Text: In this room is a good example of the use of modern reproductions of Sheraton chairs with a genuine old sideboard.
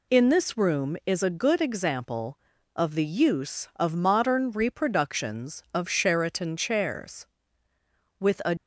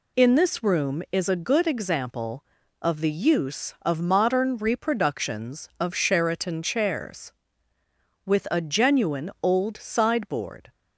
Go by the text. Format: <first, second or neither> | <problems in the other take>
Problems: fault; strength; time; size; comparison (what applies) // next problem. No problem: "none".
second | stops before "genuine old sideboard"; at 8.5 s